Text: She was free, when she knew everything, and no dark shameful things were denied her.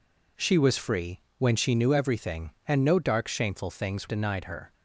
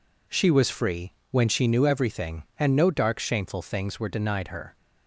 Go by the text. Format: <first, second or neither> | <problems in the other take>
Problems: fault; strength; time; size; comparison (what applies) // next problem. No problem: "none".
second | skips "were"; at 4.0 s